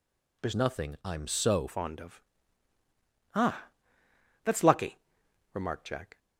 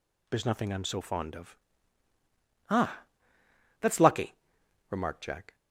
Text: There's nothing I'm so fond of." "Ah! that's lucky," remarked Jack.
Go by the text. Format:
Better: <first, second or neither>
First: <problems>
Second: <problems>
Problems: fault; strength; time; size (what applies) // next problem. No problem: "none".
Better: second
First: changes voice from "nothing" to "so"; from 0.5 to 1.6 s; 1.1 s long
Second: none